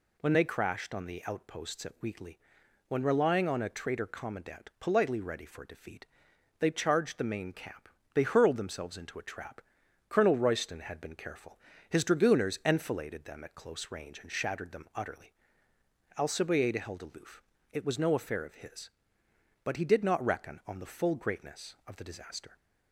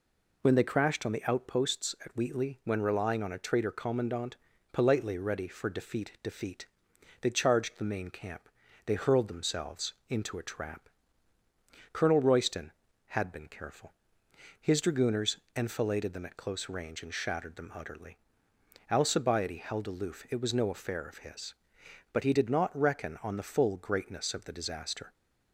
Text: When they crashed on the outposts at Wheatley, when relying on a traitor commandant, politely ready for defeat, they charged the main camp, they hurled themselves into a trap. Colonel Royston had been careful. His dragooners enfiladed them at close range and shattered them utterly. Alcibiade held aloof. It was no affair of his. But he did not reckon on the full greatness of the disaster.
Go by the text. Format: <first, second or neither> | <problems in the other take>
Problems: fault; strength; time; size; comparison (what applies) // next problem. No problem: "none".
first | says "defeat" twice; at 6.2 s // pauses between "themselves" and "into"; slight; at 9.9 s; 0.16 s long // pauses between "dragooners" and "enfiladed"; slight; at 15.3 s; 0.20 s long